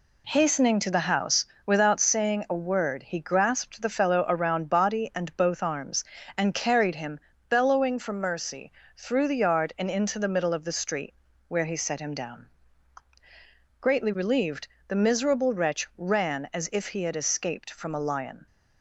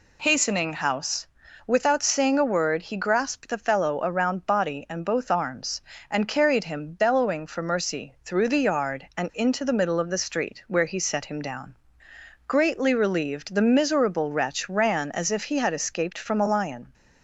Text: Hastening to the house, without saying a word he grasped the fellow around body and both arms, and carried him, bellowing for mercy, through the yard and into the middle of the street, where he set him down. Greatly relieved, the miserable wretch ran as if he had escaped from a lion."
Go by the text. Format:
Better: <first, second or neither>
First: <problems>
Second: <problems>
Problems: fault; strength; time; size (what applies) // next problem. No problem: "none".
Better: first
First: none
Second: skips "to the"; at 0.7 s